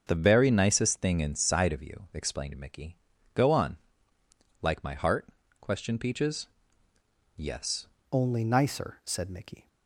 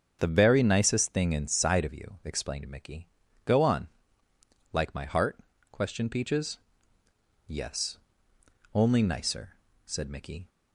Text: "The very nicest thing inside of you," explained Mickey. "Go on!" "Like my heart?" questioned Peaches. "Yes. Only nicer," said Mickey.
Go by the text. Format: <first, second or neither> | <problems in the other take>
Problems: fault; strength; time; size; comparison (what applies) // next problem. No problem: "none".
second | starts louder than the rest; until 1.0 s; 6.5 dB; also in the second // changes voice at "Only"; from 8.1 s on; 1.5 s long